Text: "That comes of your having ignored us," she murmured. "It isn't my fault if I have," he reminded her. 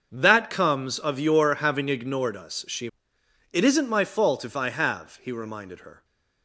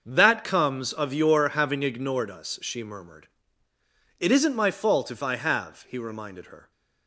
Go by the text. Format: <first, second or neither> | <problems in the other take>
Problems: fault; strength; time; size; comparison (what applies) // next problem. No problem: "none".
second | starts louder than the rest; until 1.1 s; 6.5 dB; also in the second // skips "murmured"; at 3.1 s